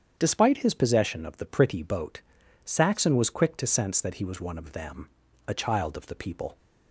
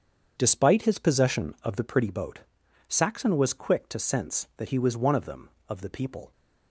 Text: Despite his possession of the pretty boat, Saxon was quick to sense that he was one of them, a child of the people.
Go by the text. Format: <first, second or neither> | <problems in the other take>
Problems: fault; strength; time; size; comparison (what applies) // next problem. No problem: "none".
first | starts louder than the rest; strong; until 1.3 s; 7.5 dB; strong in the first // skips "a child"; at 5.5 s